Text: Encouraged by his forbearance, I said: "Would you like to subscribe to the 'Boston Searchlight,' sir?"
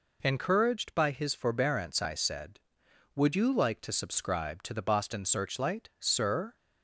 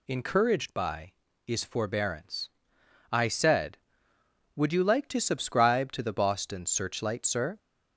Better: first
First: none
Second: says "is" for "his"; at 1.4 s

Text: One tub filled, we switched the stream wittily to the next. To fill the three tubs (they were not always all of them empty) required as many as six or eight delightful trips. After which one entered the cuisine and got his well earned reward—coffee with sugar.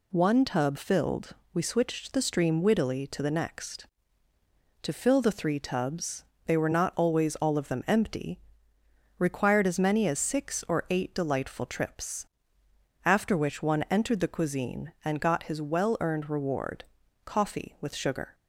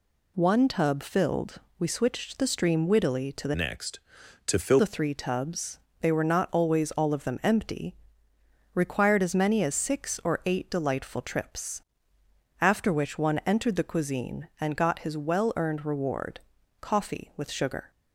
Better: first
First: none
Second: changes voice from "next" to "fill"; from 3.5 to 4.8 s; 1.3 s long

